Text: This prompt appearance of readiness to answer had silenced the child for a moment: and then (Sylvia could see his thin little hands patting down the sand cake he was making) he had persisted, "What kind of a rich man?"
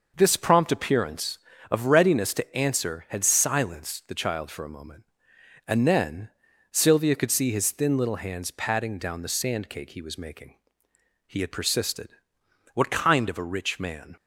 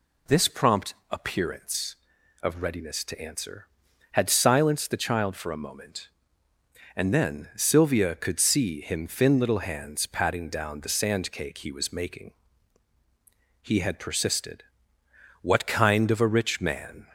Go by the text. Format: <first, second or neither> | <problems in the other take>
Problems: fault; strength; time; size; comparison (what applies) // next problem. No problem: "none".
first | pauses between "prompt" and "appearance"; slight; at 0.9 s; 0.18 s long // says "him" for "his"; at 8.7 s